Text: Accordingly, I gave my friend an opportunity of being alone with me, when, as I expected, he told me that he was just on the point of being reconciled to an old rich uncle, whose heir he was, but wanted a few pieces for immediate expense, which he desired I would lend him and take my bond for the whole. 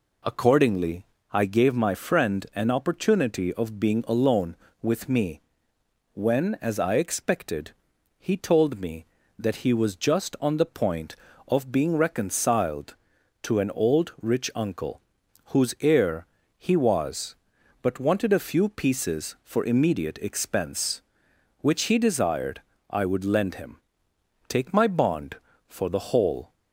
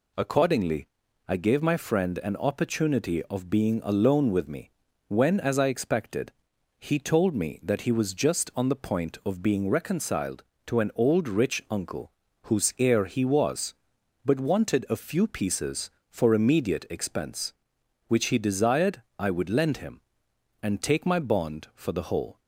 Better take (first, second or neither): second